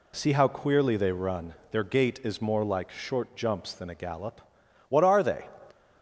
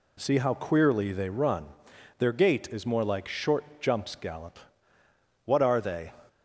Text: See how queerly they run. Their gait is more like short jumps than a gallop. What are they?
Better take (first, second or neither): first